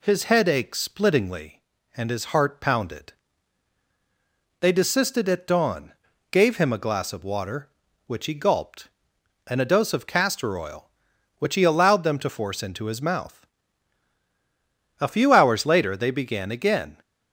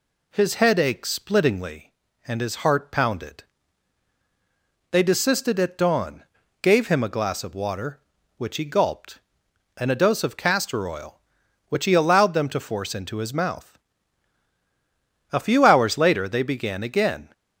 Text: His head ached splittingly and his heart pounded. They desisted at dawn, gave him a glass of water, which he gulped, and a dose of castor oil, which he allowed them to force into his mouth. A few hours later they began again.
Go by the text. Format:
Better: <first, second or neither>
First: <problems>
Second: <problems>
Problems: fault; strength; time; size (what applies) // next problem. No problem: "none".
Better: neither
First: none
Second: none